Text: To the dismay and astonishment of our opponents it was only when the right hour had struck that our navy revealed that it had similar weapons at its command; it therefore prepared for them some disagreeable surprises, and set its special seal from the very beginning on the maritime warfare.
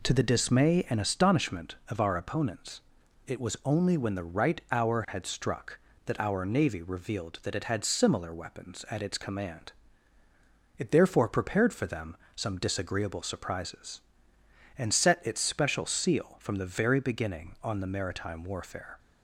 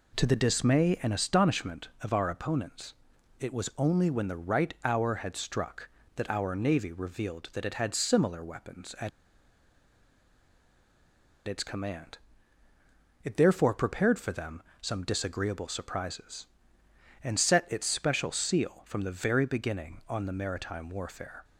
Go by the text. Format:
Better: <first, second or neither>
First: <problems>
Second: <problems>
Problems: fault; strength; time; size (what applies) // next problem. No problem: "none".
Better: first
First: pauses between "opponents" and "it"; noticeable; at 2.8 s; 0.46 s long // pauses between "them" and "some"; slight; at 12.1 s; 0.18 s long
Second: pauses between "opponents" and "it"; noticeable; at 2.9 s; 0.46 s long // pauses between "at" and "its"; strong; at 9.0 s; 2.3 s long // pauses between "them" and "some"; slight; at 14.6 s; 0.18 s long